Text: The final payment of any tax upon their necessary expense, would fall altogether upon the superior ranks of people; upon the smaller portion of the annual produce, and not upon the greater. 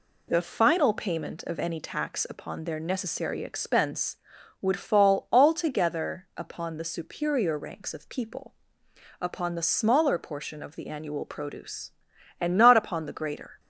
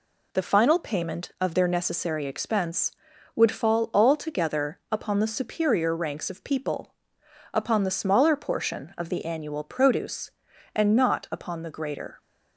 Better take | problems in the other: first | skips "any tax upon"; at 1.5 s

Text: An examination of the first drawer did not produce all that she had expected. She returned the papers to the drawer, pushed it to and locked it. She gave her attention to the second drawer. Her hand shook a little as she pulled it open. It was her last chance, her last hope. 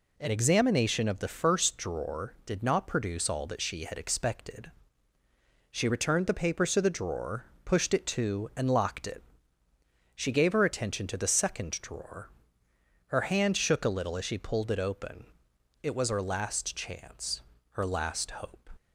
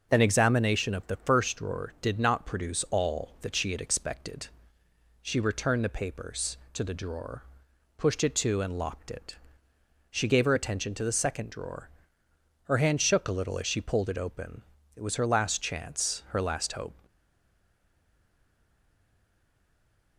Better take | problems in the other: first | stays silent after the last word; strong; from 17.0 s on; 3.1 s long

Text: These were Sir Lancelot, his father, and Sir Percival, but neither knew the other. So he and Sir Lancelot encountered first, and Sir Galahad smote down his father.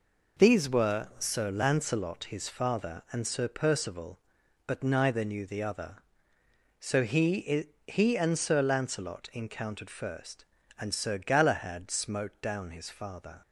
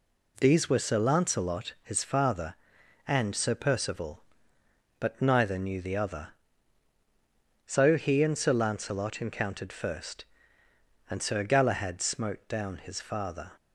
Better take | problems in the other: second | says "he" twice; at 7.8 s

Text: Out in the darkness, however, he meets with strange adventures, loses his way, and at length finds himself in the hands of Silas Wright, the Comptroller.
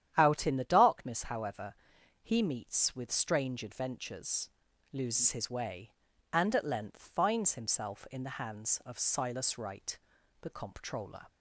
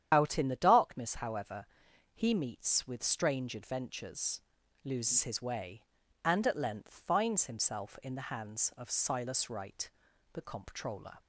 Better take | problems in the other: first | loses the start of "Out"; at 0.1 s; 50 ms // starts louder than the rest; strong; until 1.1 s; 9.5 dB; strong in the first

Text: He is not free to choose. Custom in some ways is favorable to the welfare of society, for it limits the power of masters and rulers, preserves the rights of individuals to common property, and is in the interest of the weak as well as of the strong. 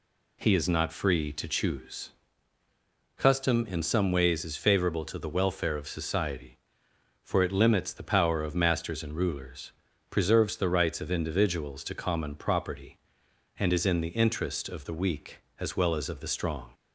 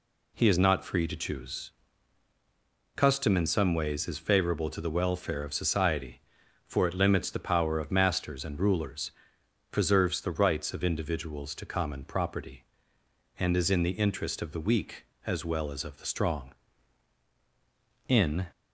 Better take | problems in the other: first | goes on to say "In"; slight; from 18.0 s on; 0.40 s long

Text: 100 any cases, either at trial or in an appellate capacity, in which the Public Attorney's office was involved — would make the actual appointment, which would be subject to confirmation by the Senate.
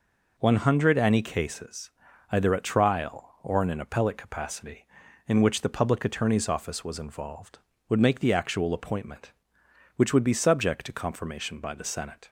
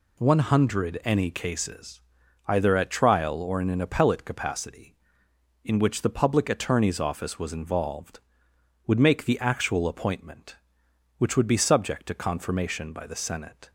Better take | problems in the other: neither | none

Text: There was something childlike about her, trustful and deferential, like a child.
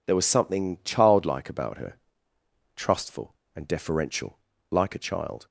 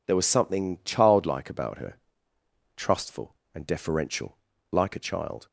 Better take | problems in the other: neither | none

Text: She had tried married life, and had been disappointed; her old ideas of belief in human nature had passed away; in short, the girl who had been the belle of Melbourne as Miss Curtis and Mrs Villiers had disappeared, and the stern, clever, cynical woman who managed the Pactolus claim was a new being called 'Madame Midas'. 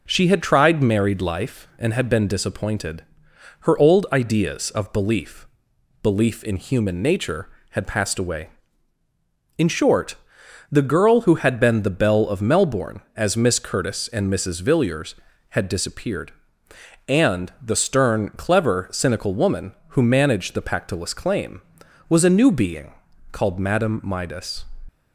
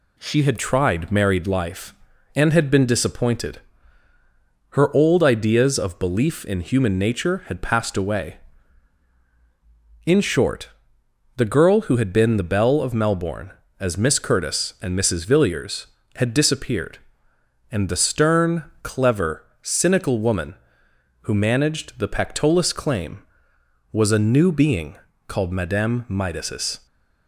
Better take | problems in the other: second | says "belief" twice; at 6.0 s // pauses between "being" and "called"; at 22.9 s; 0.38 s long; slight in the second

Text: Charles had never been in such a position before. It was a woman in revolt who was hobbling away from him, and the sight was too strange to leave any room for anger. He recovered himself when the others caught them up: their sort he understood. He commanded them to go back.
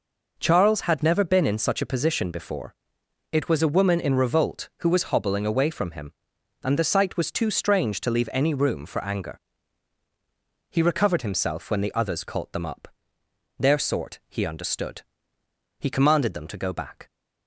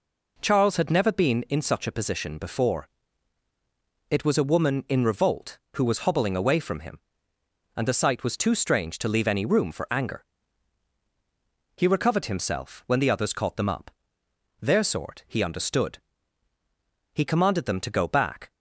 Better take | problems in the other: neither | none

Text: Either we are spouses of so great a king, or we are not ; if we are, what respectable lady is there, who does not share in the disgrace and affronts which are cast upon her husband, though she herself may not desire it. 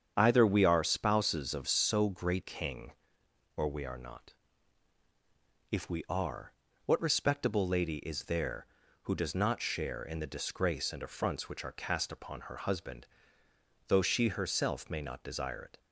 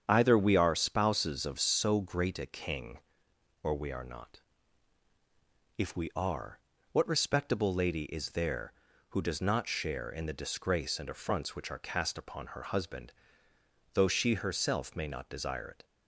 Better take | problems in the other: second | starts louder than the rest; strong; until 1.1 s; 8 dB; strong in the second // skips "a"; at 2.4 s

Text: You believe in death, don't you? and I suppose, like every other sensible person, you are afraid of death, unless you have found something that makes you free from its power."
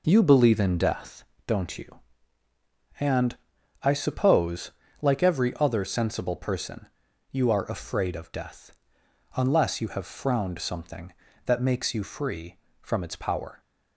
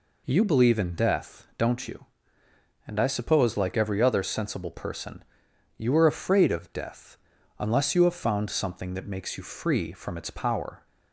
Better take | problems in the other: second | pauses between "and" and "I"; at 3.3 s; 0.44 s long // says "frowned" for "found"; at 10.0 s

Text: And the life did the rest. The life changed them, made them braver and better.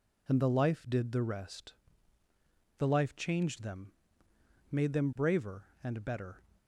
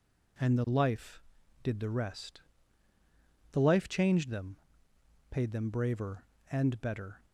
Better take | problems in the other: first | says "paid" for "made"; at 5.3 s

